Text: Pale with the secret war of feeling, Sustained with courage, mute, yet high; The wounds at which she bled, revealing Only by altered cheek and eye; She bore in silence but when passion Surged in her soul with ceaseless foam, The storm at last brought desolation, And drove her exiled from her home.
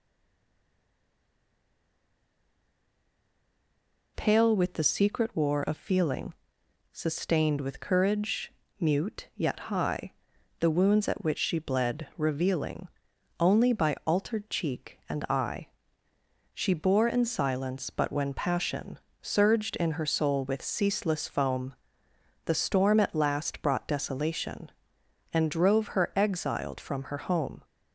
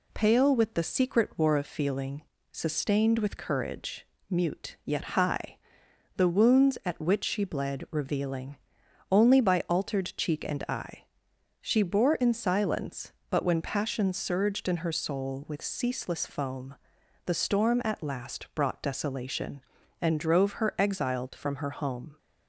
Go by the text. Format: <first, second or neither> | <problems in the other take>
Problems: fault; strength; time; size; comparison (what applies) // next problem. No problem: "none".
second | stays silent before the first word; strong; until 4.1 s; 4.1 s long // pauses between "revealing" and "Only"; noticeable; at 12.8 s; 0.50 s long; noticeable in the second // pauses between "passion" and "Surged"; slight; at 18.9 s; 0.22 s long